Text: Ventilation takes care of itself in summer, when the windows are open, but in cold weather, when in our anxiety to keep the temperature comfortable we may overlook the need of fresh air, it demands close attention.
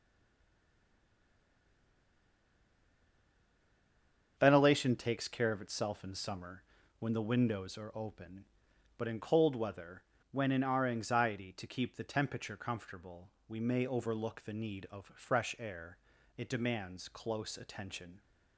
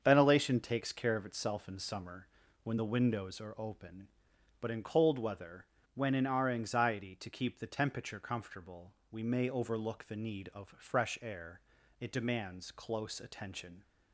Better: second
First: stays silent before the first word; strong; until 4.3 s; 4.3 s long // starts louder than the rest; until 5.3 s; 7 dB // pauses between "comfortable" and "we"; slight; at 13.2 s; 0.20 s long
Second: starts louder than the rest; until 1.0 s; 7 dB // pauses between "comfortable" and "we"; slight; at 8.9 s; 0.20 s long

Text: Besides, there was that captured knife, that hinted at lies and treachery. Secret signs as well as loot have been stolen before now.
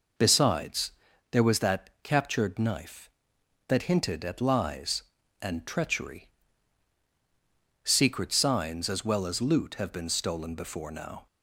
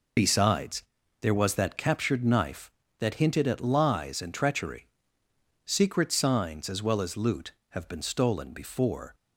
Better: first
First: none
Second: stops before "now"; at 9.1 s

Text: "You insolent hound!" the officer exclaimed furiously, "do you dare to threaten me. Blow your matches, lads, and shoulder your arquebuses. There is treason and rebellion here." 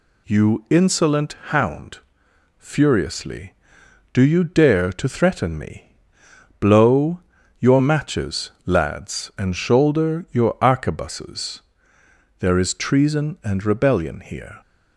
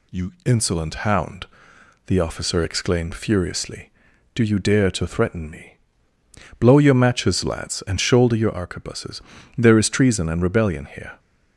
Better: second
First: skips "the officer exclaimed"; at 2.2 s // pauses between "Blow" and "your"; at 7.1 s; 0.38 s long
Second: none

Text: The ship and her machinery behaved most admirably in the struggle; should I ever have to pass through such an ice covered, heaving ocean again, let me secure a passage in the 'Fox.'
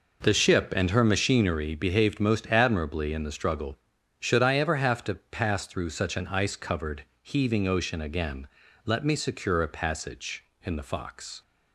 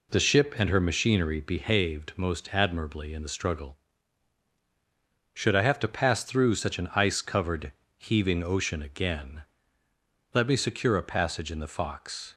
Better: first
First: none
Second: skips "ever"; at 5.6 s

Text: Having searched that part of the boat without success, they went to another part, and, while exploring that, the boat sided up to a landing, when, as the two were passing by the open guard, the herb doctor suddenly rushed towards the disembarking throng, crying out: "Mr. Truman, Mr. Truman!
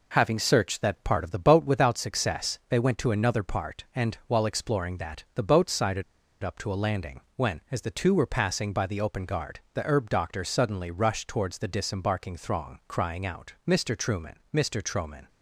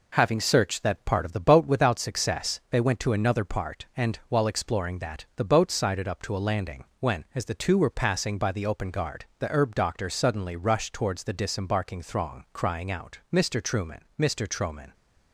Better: second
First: pauses between "sided" and "up"; at 6.0 s; 0.40 s long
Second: none

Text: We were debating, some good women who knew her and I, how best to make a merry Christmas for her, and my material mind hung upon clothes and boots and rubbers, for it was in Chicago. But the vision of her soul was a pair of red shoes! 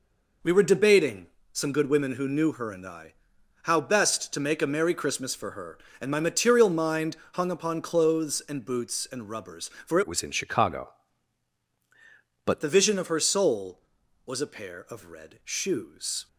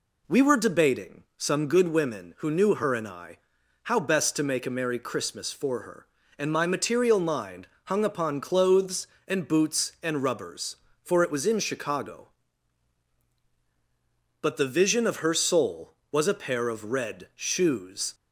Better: second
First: pauses between "mind" and "hung"; slight; at 7.1 s; 0.16 s long // changes voice from "it" to "But"; from 10.0 to 12.6 s; 2.6 s long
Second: pauses between "mind" and "hung"; slight; at 7.6 s; 0.18 s long

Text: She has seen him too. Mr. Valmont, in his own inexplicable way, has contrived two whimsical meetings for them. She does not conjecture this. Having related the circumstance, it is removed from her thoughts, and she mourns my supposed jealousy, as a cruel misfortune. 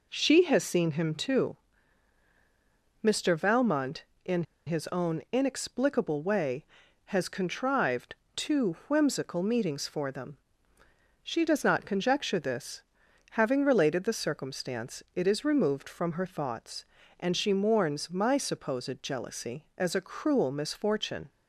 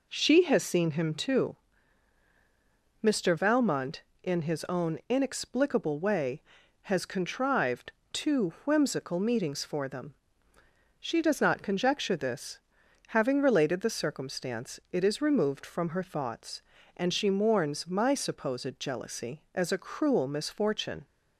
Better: second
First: pauses between "in" and "his"; slight; at 4.4 s; 0.22 s long // pauses between "contrived" and "two"; slight; at 8.1 s; 0.22 s long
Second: pauses between "contrived" and "two"; slight; at 7.9 s; 0.22 s long

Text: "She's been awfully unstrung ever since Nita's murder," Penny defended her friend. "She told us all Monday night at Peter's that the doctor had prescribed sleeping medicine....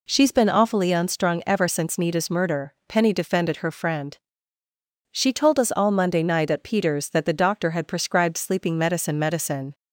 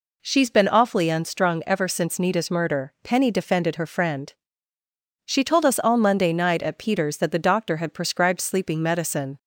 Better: second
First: says "medicine" twice; at 9.1 s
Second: none

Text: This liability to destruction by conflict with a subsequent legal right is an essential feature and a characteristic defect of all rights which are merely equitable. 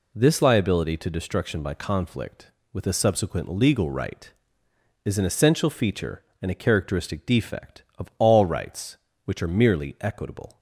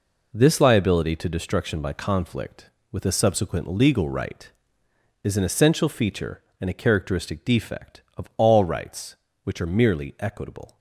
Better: first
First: none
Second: gets quieter; strong; throughout; 9 dB

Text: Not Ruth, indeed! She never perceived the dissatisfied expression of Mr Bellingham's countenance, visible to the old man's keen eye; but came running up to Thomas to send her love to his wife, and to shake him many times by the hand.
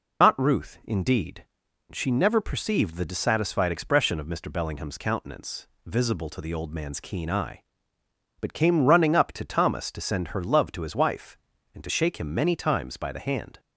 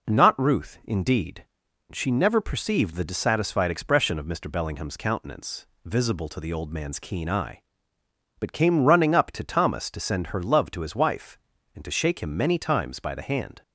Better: second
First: loses the start of "Not"; at 0.2 s; 135 ms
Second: none

